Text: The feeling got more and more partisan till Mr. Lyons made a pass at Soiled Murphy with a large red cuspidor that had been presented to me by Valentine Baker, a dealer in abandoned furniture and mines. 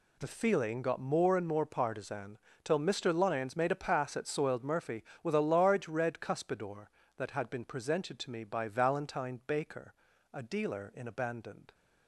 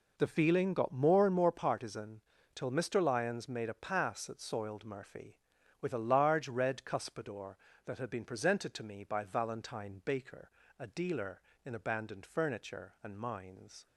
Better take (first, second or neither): second